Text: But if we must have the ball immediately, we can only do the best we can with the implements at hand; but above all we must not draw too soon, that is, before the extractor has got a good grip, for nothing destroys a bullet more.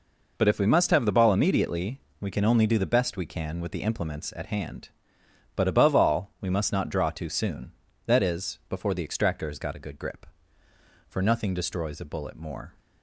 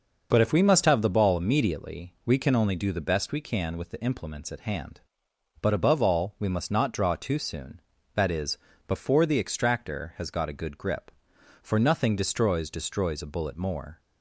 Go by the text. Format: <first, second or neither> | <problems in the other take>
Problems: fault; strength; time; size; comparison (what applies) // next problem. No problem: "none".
first | starts louder than the rest; until 1.3 s; 6 dB // says "destroys" twice; at 12.6 s